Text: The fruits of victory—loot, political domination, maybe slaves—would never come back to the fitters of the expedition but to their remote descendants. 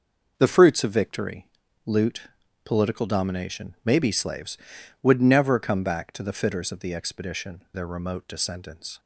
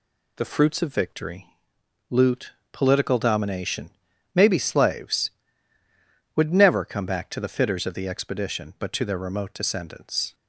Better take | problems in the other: second | skips "but to"; at 7.6 s

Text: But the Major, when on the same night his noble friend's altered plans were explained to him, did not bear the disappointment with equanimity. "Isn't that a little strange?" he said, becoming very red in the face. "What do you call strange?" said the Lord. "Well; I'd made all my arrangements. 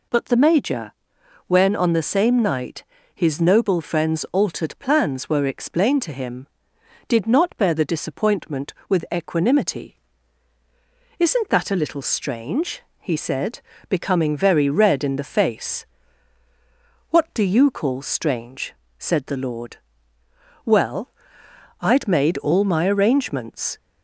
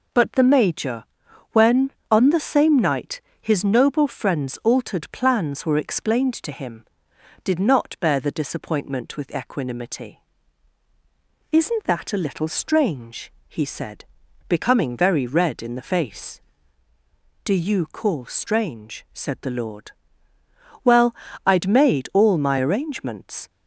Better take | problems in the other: first | pauses between "night" and "his"; slight; at 3.2 s; 0.20 s long; slight in the first // skips "What"; at 16.9 s

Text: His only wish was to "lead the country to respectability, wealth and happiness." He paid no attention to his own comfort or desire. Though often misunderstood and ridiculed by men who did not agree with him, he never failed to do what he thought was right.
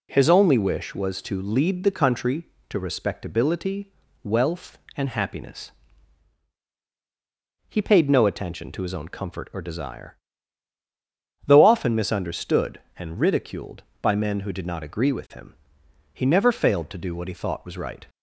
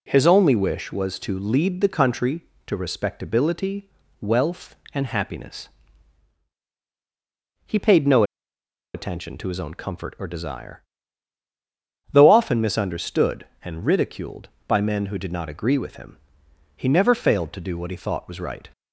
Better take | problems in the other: first | pauses between "no" and "attention"; noticeable; at 8.2 s; 0.71 s long

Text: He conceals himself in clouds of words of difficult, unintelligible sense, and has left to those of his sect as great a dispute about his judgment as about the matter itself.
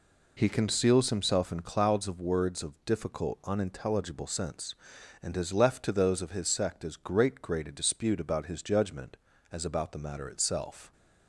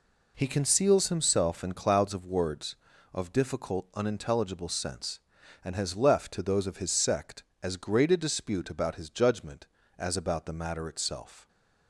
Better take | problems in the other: second | says "great" twice; at 7.4 s

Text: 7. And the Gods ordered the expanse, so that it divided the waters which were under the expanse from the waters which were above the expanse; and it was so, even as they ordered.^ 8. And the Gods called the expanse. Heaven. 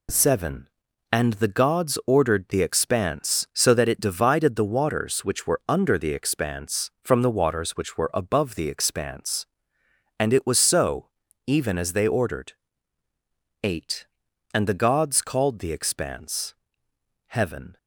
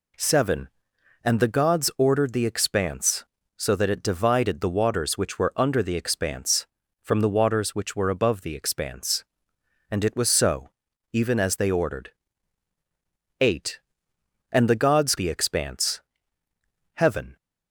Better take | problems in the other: first | skips "called"; at 15.1 s

